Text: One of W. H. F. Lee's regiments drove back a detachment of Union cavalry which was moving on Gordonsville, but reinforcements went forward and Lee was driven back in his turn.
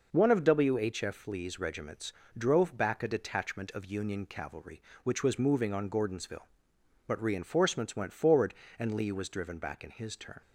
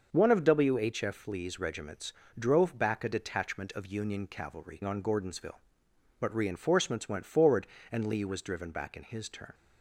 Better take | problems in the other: first | starts louder than the rest; until 1.1 s; 6 dB // pauses between "regiments" and "drove"; slight; at 2.1 s; 0.24 s long; slight in the first // skips "which was moving"; at 4.8 s

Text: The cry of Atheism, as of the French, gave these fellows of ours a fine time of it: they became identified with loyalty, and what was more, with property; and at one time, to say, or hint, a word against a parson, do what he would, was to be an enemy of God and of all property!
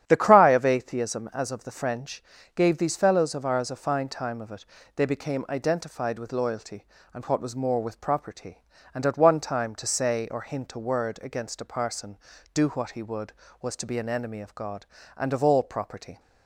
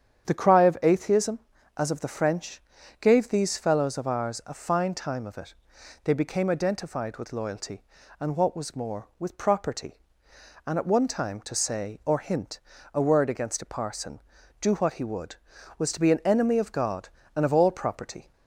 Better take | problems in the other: neither | starts louder than the rest; strong; the same in both

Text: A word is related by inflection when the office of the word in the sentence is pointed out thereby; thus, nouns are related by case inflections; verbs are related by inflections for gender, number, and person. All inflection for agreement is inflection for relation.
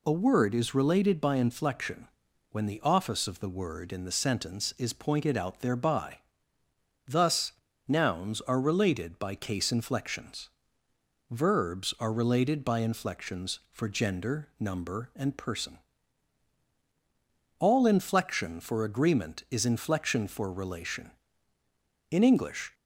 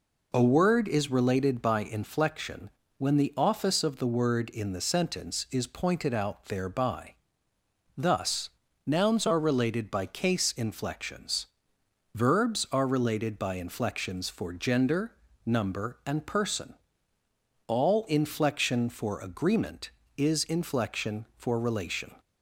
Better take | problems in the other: second | pauses between "inflection" and "when"; at 2.0 s; 0.42 s long; slight in the second // goes on to say "In English"; noticeable; from 22.0 s on; 0.64 s long

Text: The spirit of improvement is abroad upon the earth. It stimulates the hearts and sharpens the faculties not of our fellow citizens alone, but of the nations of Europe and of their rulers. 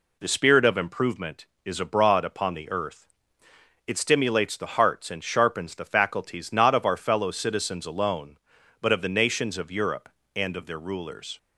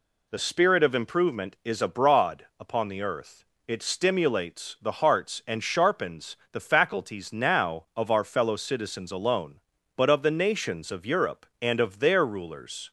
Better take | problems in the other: first | pauses between "abroad" and "upon"; slight; at 2.4 s; 0.16 s long // pauses between "sharpens" and "the"; slight; at 6.3 s; 0.16 s long // says "now" for "not"; at 7.3 s

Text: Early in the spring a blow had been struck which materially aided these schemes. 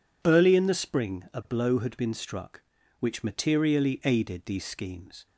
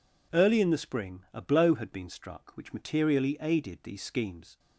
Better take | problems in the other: neither | none

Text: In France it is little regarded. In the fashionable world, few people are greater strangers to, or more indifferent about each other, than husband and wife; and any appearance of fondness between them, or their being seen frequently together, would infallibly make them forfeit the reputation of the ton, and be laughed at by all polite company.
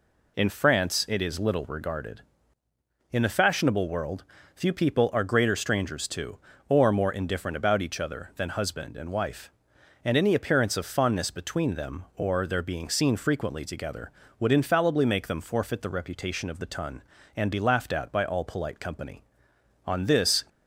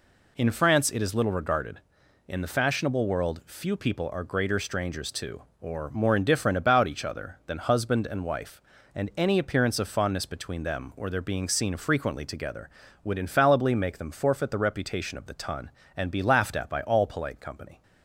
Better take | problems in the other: second | goes on to say "On this"; from 19.8 s on; 0.56 s long

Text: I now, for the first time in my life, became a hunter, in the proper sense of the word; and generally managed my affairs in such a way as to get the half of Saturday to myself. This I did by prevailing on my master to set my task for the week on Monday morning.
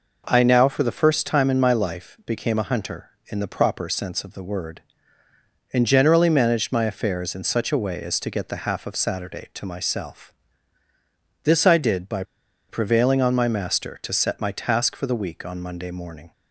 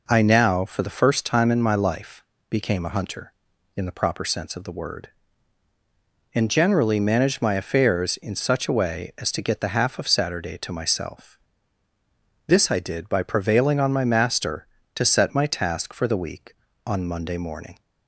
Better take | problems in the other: second | pauses between "by" and "prevailing"; noticeable; at 12.2 s; 0.46 s long

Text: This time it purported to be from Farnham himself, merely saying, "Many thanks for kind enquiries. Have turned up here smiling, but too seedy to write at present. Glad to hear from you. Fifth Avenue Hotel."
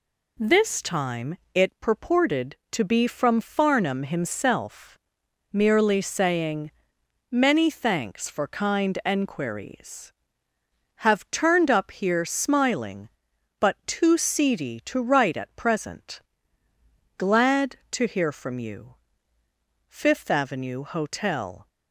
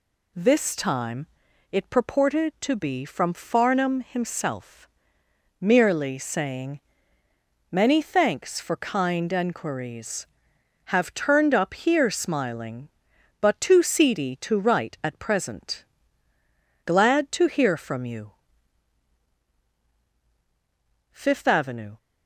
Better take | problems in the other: first | pauses between "time" and "it"; at 1.2 s; 0.44 s long; slight in the first // stops before "Hotel"; at 21.9 s

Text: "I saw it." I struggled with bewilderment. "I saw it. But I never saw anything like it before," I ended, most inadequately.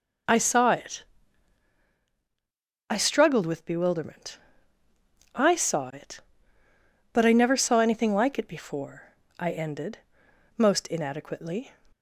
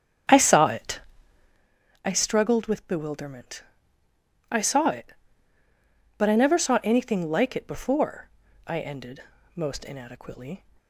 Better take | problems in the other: first | starts louder than the rest; strong; until 1.7 s; 8 dB

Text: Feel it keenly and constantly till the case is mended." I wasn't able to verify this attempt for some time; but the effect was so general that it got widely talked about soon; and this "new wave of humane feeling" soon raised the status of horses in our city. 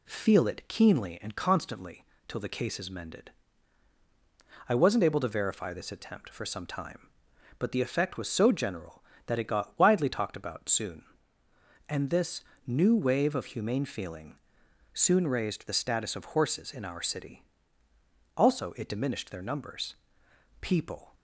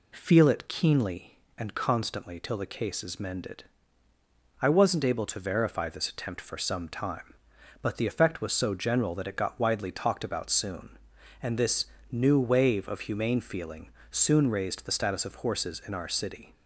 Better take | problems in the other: second | pauses between "constantly" and "till"; slight; at 2.0 s; 0.24 s long // pauses between "this" and "new"; slight; at 12.4 s; 0.24 s long; slight in the second // pauses between "feeling" and "soon"; noticeable; at 14.3 s; 0.56 s long; slight in the second // goes on to say "Also it diminished their numbers People"; strong; from 18.3 s on; 2.8 s long

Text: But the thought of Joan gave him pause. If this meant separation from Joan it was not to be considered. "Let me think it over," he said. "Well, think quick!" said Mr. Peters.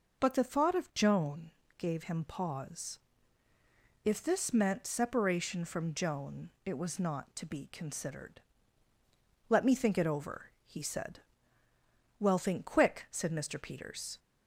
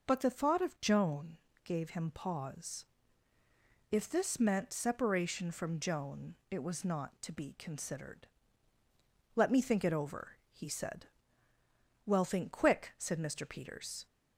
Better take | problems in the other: neither | pauses between "Joan" and "gave"; slight; the same in both // pauses between "Joan" and "it"; slight; the same in both

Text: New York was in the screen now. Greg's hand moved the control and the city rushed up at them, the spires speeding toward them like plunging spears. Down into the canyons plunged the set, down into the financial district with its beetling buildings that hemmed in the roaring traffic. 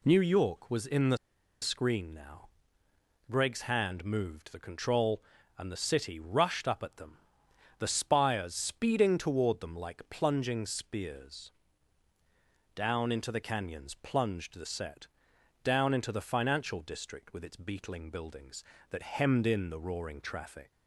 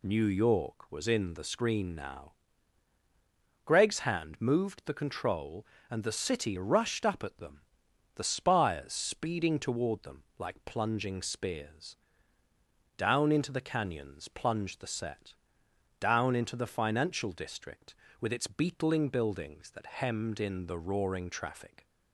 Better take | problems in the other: second | pauses between "the" and "screen"; at 1.1 s; 0.45 s long

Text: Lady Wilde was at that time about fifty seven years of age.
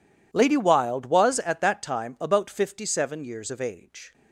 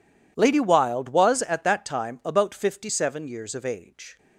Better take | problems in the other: neither | none

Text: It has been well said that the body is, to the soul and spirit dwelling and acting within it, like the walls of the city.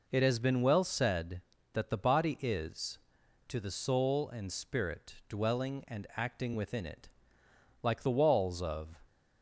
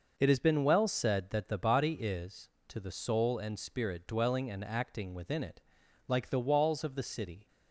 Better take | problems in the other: second | stops before "the city"; at 9.0 s

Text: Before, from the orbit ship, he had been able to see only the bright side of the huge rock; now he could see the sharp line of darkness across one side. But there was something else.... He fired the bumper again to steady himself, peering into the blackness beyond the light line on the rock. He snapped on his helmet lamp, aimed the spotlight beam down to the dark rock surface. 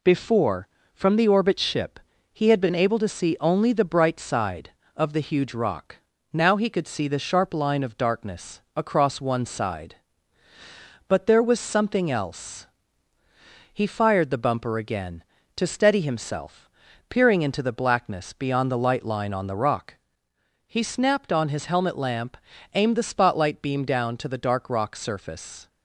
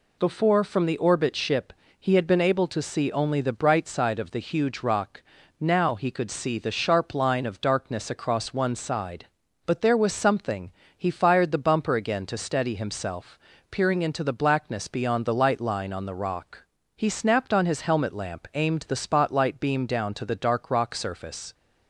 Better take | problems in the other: first | skips "else"; at 10.8 s

